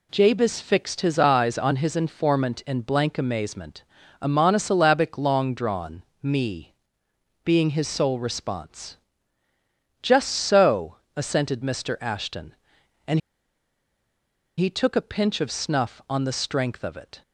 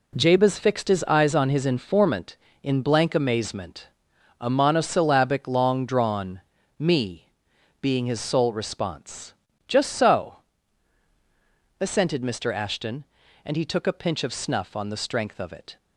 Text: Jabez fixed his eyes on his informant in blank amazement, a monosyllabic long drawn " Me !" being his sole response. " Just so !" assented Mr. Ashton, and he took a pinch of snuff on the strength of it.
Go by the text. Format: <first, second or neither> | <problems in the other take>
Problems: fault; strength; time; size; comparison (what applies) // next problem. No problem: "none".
second | pauses between "and" and "he"; strong; at 13.2 s; 1.3 s long